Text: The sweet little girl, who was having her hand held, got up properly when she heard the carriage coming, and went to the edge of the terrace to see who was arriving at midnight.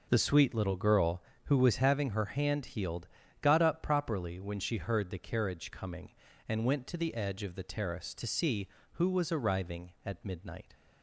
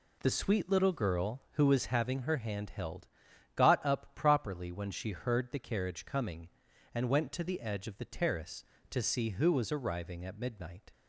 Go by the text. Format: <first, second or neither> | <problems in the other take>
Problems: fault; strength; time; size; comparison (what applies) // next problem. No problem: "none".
second | says "healed" for "held"; at 2.6 s